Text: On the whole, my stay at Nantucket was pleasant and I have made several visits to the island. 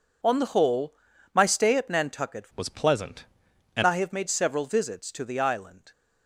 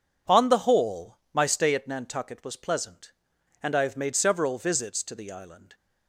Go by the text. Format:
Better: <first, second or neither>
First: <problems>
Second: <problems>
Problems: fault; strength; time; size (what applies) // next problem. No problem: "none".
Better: second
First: changes voice from "was" to "and"; from 2.5 to 3.8 s; 1.3 s long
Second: none